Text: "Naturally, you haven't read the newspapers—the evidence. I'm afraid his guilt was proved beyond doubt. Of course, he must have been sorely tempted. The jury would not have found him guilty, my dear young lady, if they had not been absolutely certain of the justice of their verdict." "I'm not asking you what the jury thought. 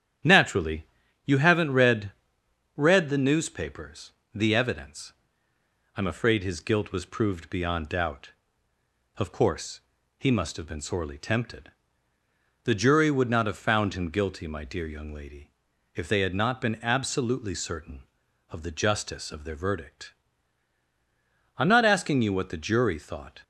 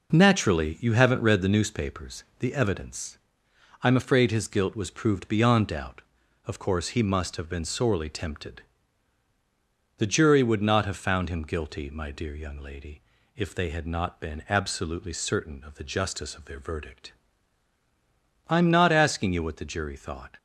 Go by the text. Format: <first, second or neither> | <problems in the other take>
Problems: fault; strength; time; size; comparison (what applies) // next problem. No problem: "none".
second | starts louder than the rest; strong; until 1.6 s; 9.5 dB // says "read" twice; at 2.7 s